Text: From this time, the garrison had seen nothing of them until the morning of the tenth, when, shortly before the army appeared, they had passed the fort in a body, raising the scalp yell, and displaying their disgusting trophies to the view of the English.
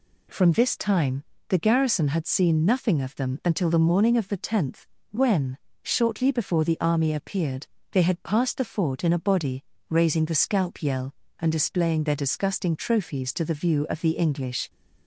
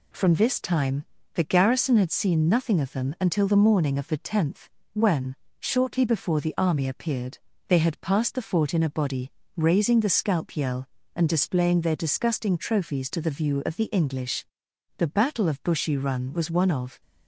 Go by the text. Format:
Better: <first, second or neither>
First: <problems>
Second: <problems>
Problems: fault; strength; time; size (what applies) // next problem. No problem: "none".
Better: first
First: none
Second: goes on to say "The battle of Bushy Run was one of"; strong; from 14.9 s on; 2.0 s long